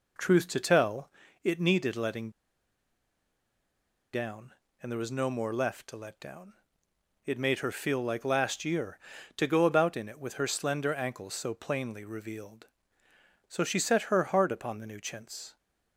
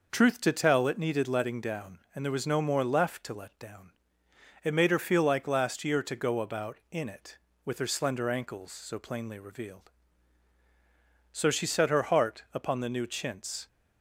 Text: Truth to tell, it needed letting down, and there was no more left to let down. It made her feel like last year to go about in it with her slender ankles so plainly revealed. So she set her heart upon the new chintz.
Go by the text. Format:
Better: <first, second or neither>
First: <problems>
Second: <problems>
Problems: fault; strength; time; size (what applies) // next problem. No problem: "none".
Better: second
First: pauses between "letting" and "down"; strong; at 2.3 s; 1.8 s long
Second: none